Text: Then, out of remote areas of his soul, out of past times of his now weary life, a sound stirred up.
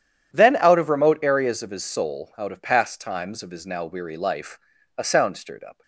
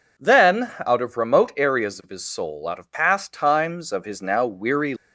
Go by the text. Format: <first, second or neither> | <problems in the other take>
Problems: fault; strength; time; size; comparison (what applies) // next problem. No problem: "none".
first | stops before "life a sound stirred up"; at 4.9 s